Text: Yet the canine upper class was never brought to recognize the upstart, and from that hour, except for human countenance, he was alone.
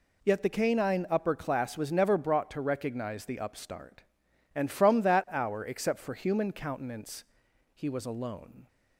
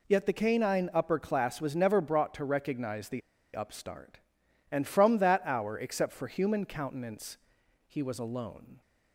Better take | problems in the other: first | pauses between "the" and "upstart"; slight; at 3.2 s; 0.35 s long

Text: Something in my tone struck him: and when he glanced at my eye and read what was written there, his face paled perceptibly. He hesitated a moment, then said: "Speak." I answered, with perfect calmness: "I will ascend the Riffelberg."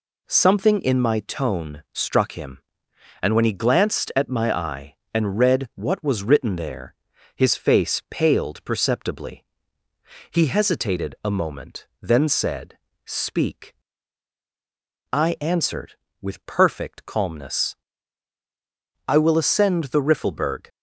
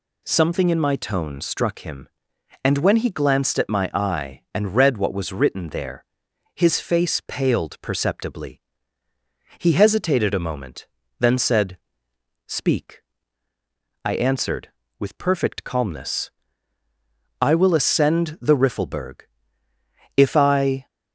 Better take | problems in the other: first | goes on to say "If I"; noticeable; from 20.1 s on; 0.70 s long

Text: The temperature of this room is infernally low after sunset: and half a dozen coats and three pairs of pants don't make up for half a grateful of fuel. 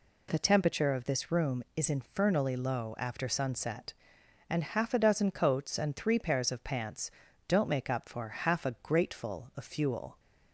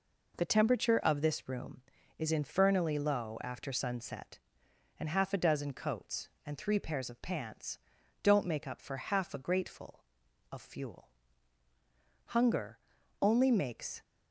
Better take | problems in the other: first | pauses between "pants" and "don't"; at 7.7 s; 0.44 s long; also in the first // goes on to say "Hunger only makes"; strong; from 12.2 s on; 1.7 s long

